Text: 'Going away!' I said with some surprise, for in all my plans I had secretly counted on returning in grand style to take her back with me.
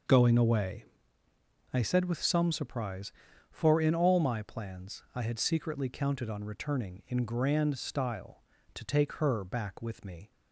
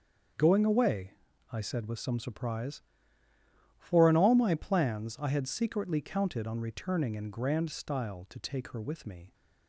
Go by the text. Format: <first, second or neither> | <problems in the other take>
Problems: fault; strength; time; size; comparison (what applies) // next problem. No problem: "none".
first | starts louder than the rest; until 1.7 s; 6.5 dB // skips "back"; at 8.8 s